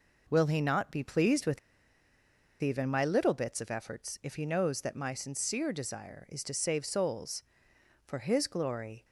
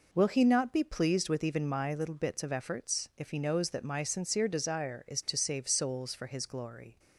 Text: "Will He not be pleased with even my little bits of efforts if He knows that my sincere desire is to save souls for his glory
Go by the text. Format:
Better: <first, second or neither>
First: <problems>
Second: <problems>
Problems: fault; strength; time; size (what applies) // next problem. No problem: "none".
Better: second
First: pauses between "with" and "even"; at 1.5 s; 1.0 s long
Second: none